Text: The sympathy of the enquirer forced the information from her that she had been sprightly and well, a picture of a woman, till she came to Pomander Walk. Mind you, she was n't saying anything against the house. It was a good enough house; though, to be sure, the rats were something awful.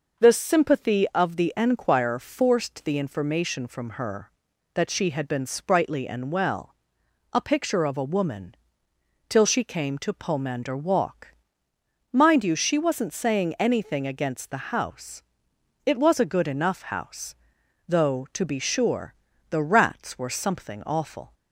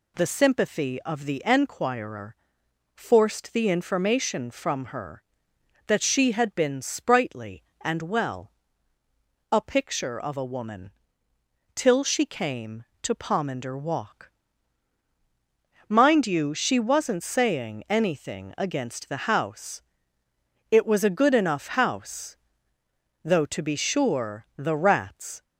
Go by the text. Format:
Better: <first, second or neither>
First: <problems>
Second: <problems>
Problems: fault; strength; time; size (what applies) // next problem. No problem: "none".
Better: first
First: none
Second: pauses between "enquirer" and "forced"; noticeable; at 2.3 s; 0.58 s long // stops before "were something awful"; at 25.4 s